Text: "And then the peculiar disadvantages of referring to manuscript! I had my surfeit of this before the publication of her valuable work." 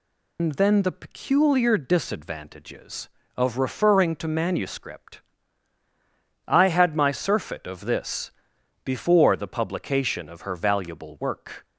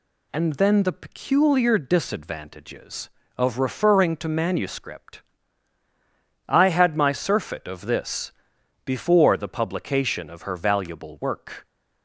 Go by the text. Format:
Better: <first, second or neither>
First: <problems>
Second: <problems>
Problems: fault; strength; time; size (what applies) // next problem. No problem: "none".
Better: second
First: loses the start of "And"; at 0.3 s; 95 ms // pauses between "this" and "before"; noticeable; at 8.3 s; 0.54 s long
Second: pauses between "this" and "before"; noticeable; at 8.3 s; 0.54 s long